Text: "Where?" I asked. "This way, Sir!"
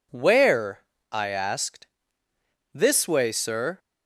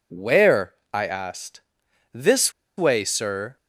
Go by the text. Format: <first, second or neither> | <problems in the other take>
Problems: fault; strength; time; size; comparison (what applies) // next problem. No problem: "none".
first | pauses between "This" and "way"; slight; at 2.5 s; 0.26 s long